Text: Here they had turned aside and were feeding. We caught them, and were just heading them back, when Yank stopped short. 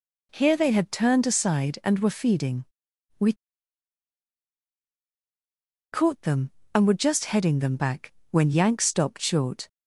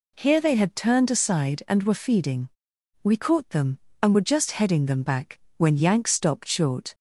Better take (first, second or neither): second